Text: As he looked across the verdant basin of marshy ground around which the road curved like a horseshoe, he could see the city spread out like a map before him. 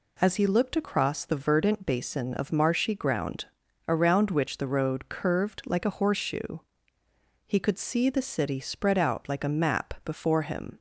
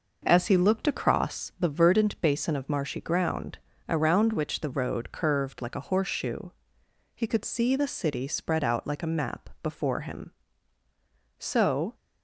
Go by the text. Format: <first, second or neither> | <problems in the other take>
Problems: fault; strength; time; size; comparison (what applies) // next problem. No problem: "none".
first | pauses between "ground" and "around"; slight; at 3.5 s; 0.32 s long; also in the first // goes on to say "So"; from 11.3 s on; 0.56 s long